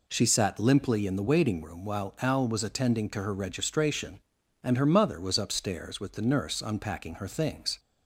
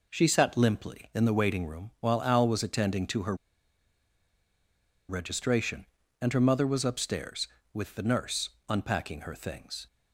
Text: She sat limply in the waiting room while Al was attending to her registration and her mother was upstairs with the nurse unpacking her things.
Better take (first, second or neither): first